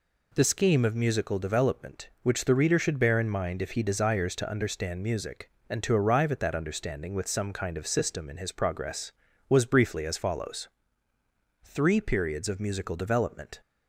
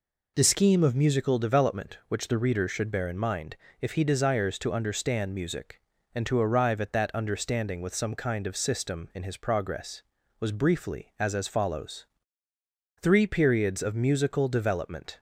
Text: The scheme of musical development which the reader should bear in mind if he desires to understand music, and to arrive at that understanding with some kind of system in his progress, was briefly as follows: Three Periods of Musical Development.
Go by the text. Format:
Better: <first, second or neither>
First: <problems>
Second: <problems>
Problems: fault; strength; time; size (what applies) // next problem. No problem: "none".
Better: first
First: none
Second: pauses between "mind" and "if"; slight; at 3.5 s; 0.24 s long // says "as" twice; at 11.3 s